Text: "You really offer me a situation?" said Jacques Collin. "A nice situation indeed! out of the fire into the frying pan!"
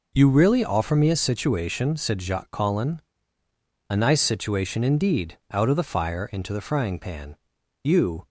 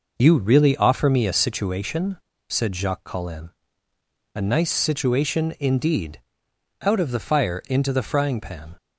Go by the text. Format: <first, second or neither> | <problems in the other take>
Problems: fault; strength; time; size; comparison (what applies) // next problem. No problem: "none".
second | goes on to say "You"; slight; from 7.8 s on; 0.44 s long